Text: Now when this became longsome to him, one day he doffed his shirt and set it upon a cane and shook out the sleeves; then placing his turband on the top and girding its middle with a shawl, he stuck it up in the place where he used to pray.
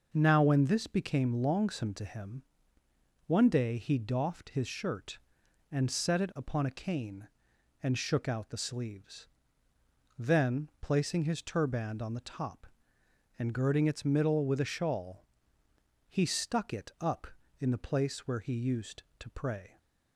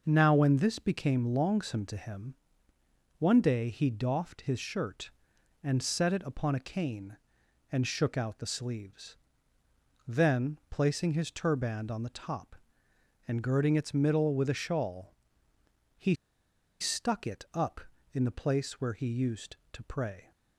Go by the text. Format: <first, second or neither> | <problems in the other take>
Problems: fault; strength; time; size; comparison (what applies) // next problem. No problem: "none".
first | pauses between "he" and "stuck"; noticeable; at 16.1 s; 0.67 s long